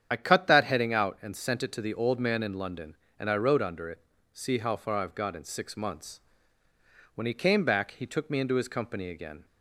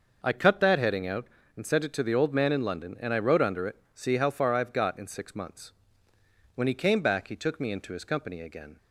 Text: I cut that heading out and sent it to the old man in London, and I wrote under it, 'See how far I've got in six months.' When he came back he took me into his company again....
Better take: second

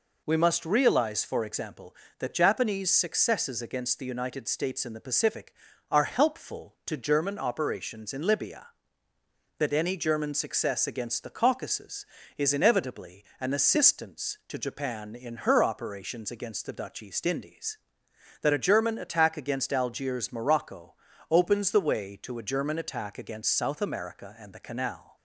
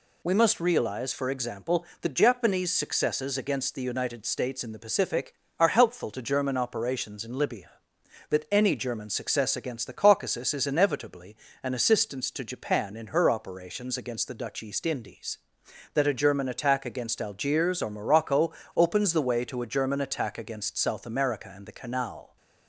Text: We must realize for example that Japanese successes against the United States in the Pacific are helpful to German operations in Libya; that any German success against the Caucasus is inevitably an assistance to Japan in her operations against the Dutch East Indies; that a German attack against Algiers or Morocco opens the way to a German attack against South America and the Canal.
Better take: second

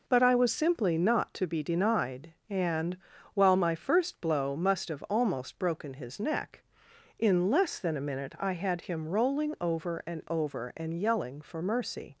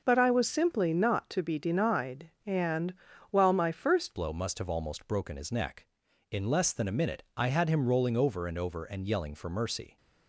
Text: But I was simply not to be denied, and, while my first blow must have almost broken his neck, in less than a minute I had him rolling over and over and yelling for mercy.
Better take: first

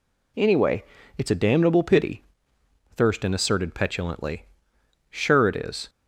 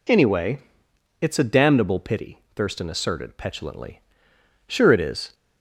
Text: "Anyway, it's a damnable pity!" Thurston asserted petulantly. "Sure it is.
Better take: neither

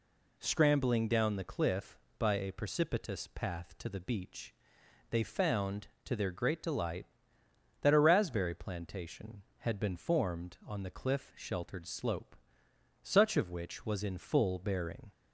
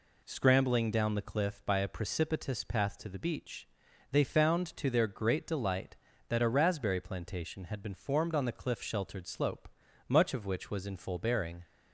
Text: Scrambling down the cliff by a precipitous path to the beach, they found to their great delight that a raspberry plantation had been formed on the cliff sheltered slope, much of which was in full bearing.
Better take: second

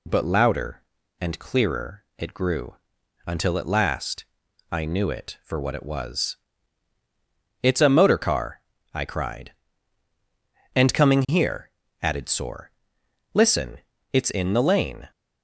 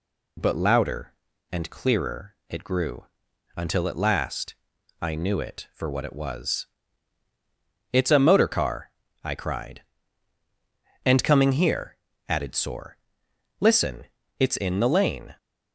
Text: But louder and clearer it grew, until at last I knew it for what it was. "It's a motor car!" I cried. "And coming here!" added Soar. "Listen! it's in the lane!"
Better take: neither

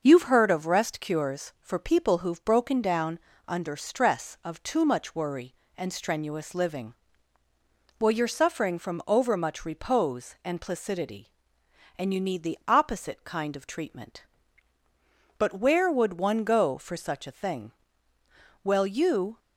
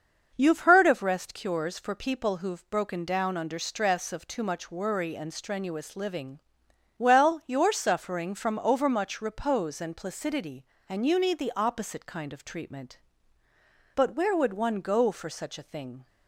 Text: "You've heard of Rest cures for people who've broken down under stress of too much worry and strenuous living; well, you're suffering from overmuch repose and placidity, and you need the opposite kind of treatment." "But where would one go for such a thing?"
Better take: second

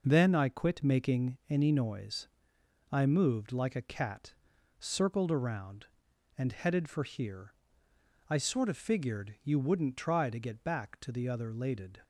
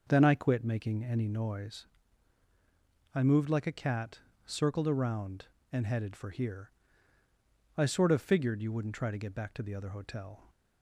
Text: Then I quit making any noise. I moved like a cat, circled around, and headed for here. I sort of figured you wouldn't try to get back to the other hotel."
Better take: second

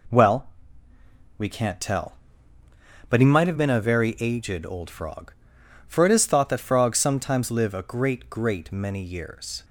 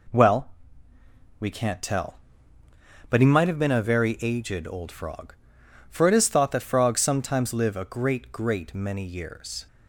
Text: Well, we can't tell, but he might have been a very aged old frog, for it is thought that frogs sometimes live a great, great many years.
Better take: neither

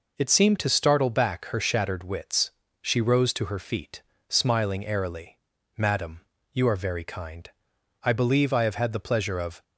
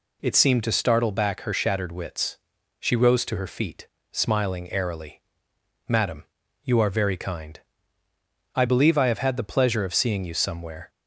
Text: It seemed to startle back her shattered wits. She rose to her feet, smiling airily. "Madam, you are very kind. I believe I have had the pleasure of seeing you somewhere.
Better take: second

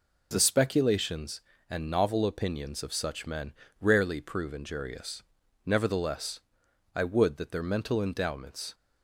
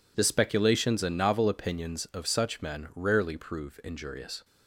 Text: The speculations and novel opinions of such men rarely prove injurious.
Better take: second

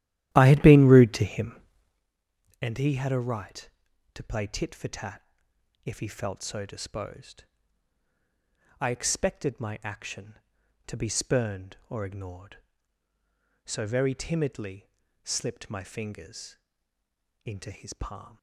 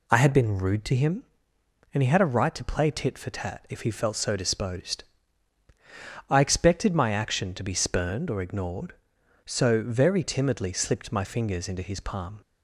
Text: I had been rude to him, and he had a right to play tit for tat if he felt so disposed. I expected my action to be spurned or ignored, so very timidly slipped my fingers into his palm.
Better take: second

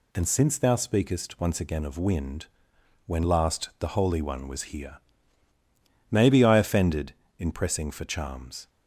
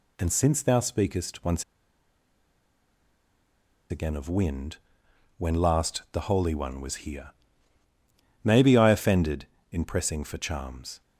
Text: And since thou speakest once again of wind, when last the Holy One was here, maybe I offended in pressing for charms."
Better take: first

